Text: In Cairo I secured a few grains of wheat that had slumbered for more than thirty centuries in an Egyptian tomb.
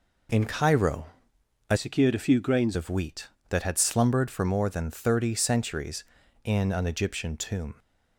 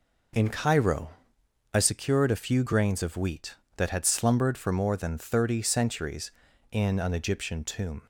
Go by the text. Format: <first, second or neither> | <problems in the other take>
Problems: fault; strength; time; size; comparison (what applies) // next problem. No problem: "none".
second | pauses between "Cairo" and "I"; noticeable; at 1.0 s; 0.62 s long; noticeable in the second // changes voice from "secured" to "grains"; from 1.7 to 2.7 s; 1.0 s long